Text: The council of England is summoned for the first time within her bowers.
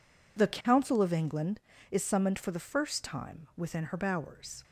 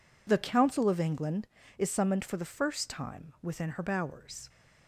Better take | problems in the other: neither | none

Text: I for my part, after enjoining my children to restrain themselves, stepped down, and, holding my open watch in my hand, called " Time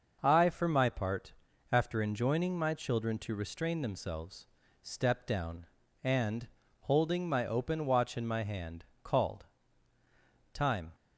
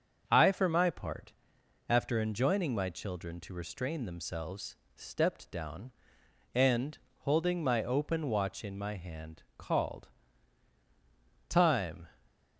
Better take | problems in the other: neither | starts louder than the rest; the same in both

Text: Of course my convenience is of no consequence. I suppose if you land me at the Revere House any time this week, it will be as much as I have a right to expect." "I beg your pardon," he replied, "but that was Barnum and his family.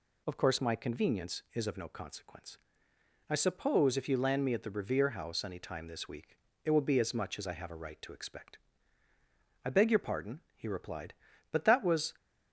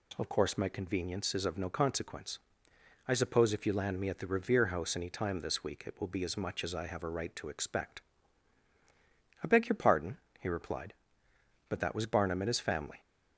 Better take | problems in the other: second | stops before "Barnum and his family"; at 12.1 s

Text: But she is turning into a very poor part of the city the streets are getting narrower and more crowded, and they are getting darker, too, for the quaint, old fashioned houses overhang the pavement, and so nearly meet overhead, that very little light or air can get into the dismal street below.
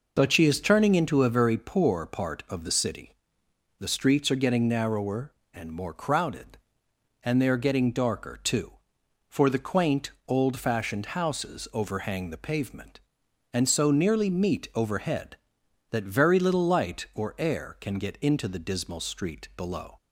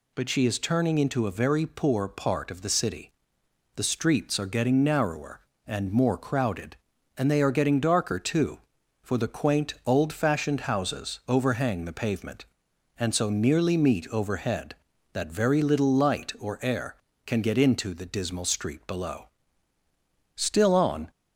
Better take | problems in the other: first | pauses between "city" and "the"; noticeable; at 3.0 s; 0.66 s long; noticeable in the first // goes on to say "Still on"; noticeable; from 20.3 s on; 0.74 s long

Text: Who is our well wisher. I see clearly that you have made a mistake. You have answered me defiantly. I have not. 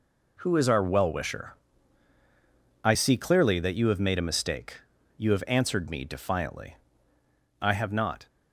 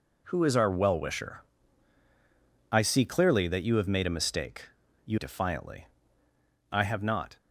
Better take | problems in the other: first | skips "have answered me"; at 5.1 s

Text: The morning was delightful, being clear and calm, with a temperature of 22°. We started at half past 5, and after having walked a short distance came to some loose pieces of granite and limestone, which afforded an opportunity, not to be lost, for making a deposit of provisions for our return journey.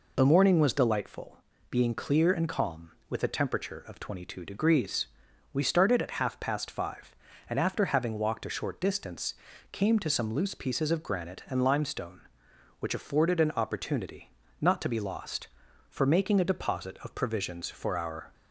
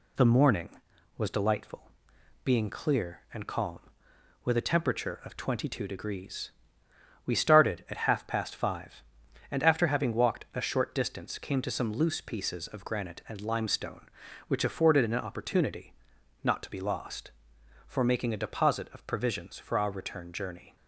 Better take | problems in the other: second | pauses between "distance" and "came"; slight; at 9.3 s; 0.36 s long // stops before "return journey"; at 18.3 s

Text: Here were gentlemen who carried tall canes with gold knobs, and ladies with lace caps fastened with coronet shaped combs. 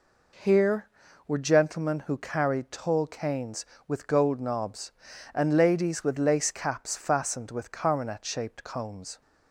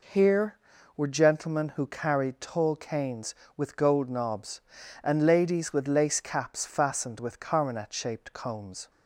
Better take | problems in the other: neither | none

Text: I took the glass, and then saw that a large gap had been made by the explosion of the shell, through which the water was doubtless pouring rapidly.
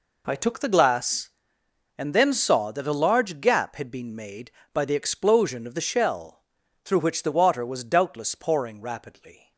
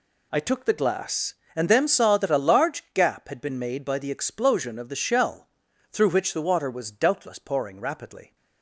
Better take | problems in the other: neither | none

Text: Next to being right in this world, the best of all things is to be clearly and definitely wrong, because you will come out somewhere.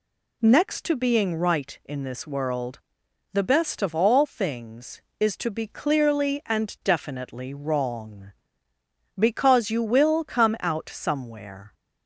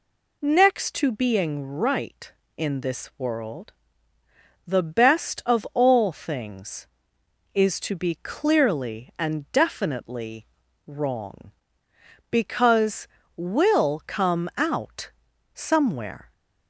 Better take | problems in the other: first | pauses between "definitely" and "wrong"; at 10.4 s; 0.40 s long // skips "you"; at 13.2 s // pauses between "out" and "somewhere"; at 15.1 s; 0.44 s long

